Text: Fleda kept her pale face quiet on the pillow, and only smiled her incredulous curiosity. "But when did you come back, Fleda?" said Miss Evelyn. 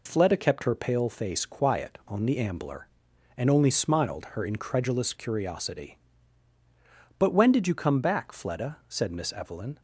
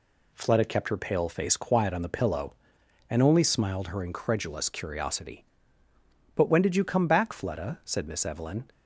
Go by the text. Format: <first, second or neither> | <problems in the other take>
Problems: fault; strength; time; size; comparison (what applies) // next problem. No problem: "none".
second | says "ambler" for "pillow"; at 2.3 s